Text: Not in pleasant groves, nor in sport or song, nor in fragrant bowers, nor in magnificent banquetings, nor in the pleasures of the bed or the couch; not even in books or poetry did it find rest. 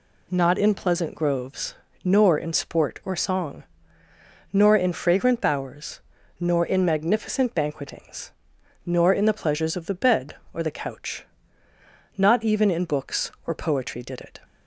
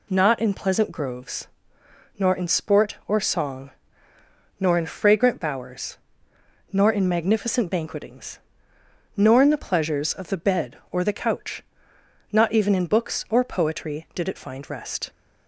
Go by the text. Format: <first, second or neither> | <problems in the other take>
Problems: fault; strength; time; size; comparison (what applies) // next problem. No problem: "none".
second | stops before "find rest"; at 14.4 s